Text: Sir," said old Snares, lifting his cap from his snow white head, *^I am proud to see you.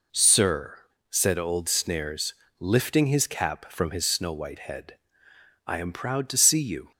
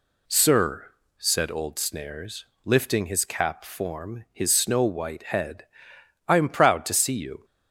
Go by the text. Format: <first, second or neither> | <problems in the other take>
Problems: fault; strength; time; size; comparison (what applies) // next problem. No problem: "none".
first | says "form" for "from"; at 3.6 s